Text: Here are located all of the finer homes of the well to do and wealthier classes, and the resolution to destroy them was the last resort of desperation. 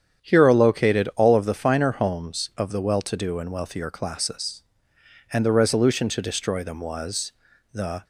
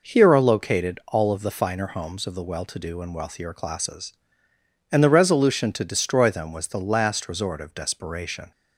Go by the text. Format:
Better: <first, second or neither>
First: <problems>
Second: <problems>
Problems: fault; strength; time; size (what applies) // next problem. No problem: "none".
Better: second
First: starts louder than the rest; strong; until 1.3 s; 8.5 dB // pauses between "was" and "the"; at 7.3 s; 0.40 s long // stops before "last resort of desperation"; at 8.0 s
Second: none